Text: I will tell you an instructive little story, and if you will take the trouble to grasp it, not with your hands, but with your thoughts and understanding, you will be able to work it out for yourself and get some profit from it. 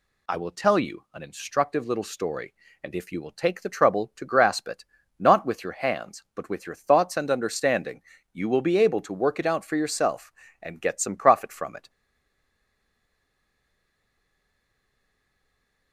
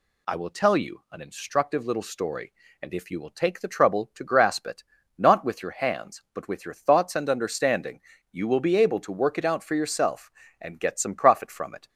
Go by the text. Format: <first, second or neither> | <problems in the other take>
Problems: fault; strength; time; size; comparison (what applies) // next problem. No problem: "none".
second | stays silent after the last word; strong; from 11.8 s on; 4.1 s long